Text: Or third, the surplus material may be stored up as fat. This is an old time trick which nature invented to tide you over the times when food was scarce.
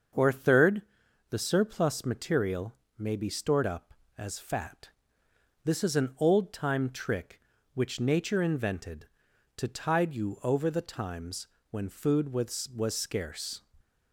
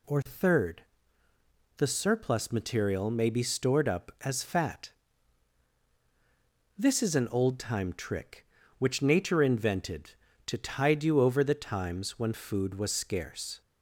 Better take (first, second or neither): second